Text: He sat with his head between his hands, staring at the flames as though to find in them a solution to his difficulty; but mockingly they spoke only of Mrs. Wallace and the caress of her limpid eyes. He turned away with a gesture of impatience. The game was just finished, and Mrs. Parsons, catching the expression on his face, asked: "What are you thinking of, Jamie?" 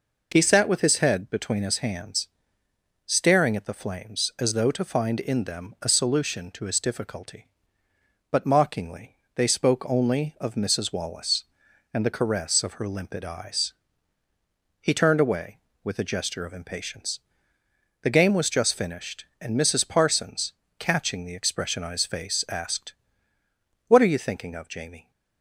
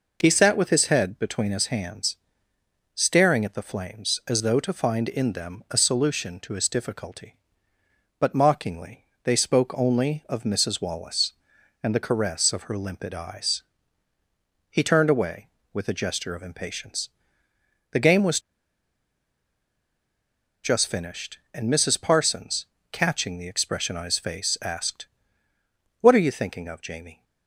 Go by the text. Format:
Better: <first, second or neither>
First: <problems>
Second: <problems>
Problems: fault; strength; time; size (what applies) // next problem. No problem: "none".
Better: first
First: pauses between "mockingly" and "they"; slight; at 9.1 s; 0.16 s long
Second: pauses between "mockingly" and "they"; slight; at 9.0 s; 0.16 s long // pauses between "was" and "just"; strong; at 18.3 s; 2.2 s long